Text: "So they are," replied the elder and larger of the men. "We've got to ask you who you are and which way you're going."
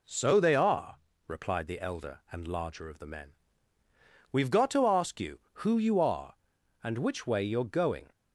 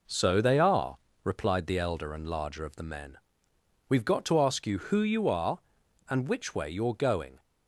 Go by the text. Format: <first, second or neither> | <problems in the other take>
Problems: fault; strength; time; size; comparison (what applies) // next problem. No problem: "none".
neither | none